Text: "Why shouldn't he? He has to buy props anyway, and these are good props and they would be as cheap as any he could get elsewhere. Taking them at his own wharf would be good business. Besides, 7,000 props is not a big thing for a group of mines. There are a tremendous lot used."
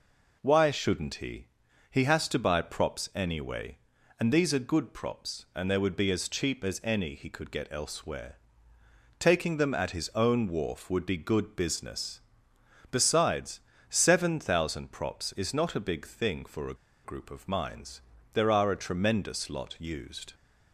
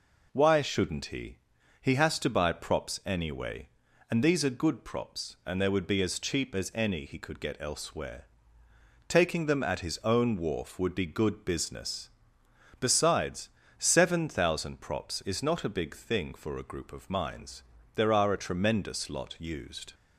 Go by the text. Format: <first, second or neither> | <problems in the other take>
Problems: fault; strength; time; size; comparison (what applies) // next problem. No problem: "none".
second | pauses between "a" and "group"; slight; at 16.7 s; 0.29 s long